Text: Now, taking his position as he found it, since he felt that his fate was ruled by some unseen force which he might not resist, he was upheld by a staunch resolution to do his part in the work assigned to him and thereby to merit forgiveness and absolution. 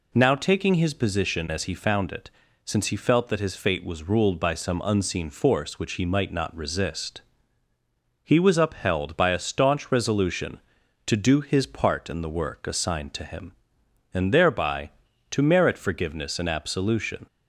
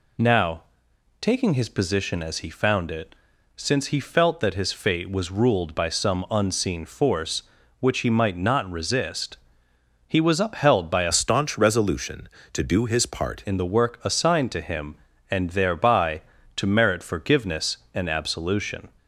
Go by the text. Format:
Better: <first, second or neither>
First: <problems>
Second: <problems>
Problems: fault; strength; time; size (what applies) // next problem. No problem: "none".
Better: first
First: none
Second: changes voice from "staunch" to "part"; from 11.1 to 13.4 s; 2.3 s long